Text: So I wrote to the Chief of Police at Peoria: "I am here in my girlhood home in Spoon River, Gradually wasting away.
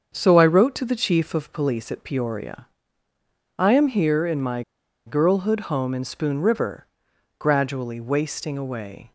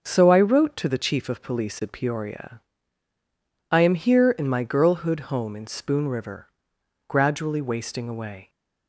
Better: second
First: starts louder than the rest; until 1.1 s; 7 dB // pauses between "my" and "girlhood"; at 4.6 s; 0.45 s long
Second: starts louder than the rest; until 1.0 s; 6.5 dB

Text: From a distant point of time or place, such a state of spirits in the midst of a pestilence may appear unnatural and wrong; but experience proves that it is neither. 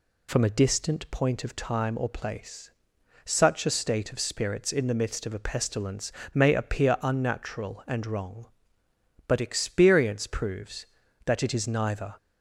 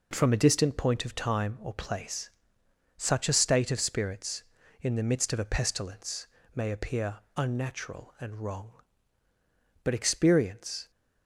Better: first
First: pauses between "pestilence" and "may"; slight; at 6.1 s; 0.24 s long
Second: pauses between "pestilence" and "may"; slight; at 6.2 s; 0.28 s long // pauses between "appear" and "unnatural"; slight; at 7.1 s; 0.18 s long // stops before "proves that it is neither"; at 10.8 s

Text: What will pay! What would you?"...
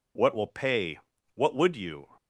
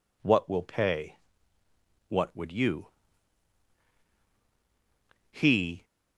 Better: first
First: none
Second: goes on to say "He"; from 5.3 s on; 0.52 s long

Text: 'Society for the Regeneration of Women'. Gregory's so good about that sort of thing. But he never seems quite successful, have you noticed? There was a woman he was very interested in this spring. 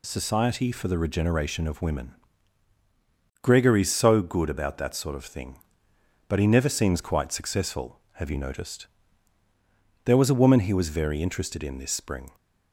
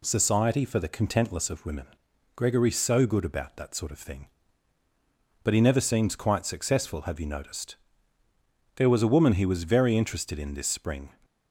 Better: first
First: none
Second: says "Contentless" for "Regeneration"; at 0.8 s

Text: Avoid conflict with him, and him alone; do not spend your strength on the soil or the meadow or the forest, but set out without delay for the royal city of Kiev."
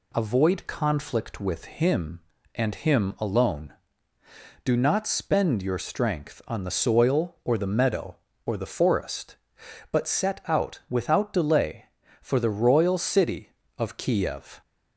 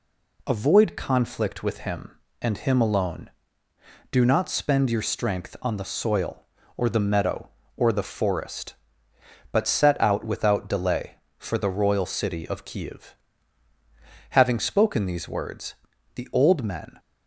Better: first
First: none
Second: goes on to say "Having spoken these words the old men"; strong; from 14.3 s on; 2.6 s long

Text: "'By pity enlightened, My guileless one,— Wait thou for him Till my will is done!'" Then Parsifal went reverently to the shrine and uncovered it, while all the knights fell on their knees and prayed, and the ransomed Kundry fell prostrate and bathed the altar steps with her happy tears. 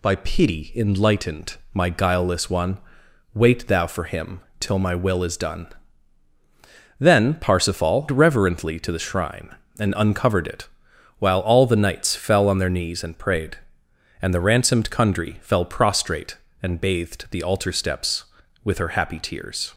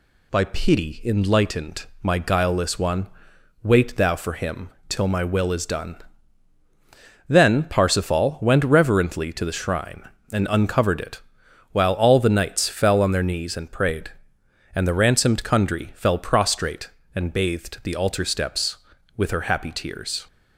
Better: second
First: pauses between "him" and "Till"; slight; at 4.4 s; 0.18 s long // skips "went"; at 8.0 s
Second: pauses between "him" and "Till"; slight; at 4.6 s; 0.18 s long

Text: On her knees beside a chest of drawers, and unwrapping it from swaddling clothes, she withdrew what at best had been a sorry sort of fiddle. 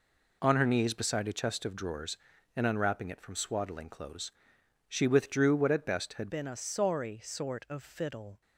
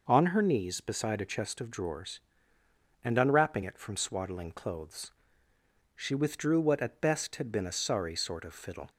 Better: second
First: changes voice at "been"; from 6.2 s on; 2.2 s long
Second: none

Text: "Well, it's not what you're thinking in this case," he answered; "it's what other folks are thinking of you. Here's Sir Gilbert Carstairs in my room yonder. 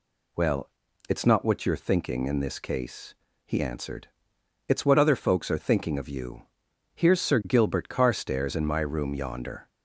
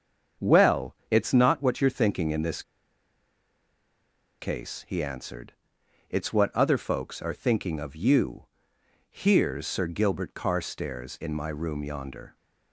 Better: first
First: none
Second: starts louder than the rest; strong; until 1.5 s; 7 dB // pauses between "this" and "case"; strong; at 2.6 s; 1.7 s long

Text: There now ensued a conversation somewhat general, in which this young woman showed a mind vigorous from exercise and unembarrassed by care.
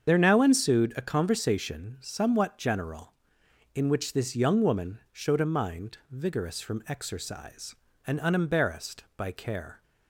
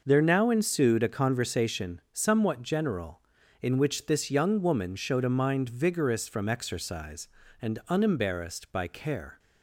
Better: second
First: loses the start of "There"; at 0.0 s; 55 ms // starts louder than the rest; strong; until 1.1 s; 7.5 dB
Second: none

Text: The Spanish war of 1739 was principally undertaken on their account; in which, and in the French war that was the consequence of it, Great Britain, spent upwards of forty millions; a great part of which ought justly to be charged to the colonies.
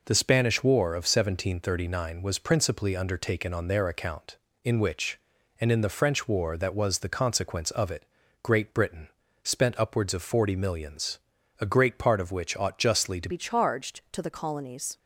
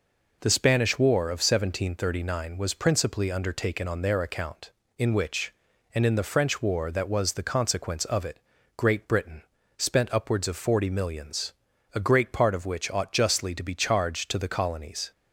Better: second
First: changes voice at "be"; from 13.2 s on; 1.7 s long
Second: none

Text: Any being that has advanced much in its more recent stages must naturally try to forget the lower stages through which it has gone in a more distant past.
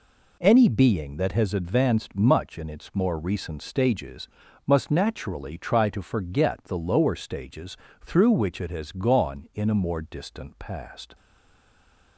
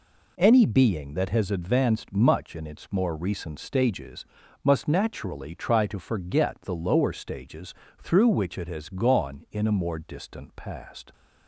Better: second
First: pauses between "stages" and "must"; at 4.2 s; 0.40 s long // pauses between "stages" and "through"; slight; at 7.7 s; 0.30 s long // stays silent after the last word; from 11.1 s on; 1.0 s long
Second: pauses between "stages" and "must"; at 4.2 s; 0.40 s long // pauses between "stages" and "through"; slight; at 7.7 s; 0.30 s long

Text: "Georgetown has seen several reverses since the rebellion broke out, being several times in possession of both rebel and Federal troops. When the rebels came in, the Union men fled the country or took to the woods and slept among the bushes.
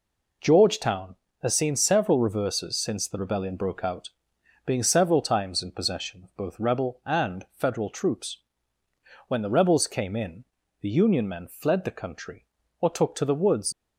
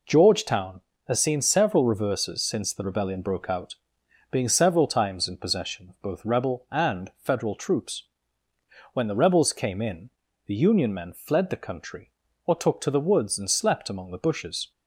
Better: second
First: stops before "and slept among the bushes"; at 13.7 s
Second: none

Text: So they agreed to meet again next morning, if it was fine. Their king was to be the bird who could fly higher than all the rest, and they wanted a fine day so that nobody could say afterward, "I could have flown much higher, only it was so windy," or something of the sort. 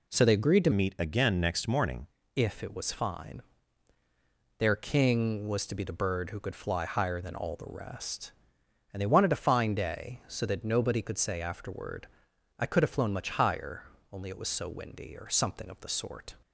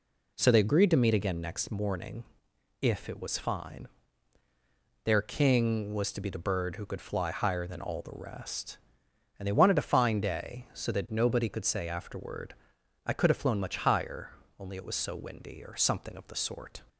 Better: second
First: changes voice from "meet" to "morning"; from 0.7 to 2.0 s; 1.3 s long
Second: none

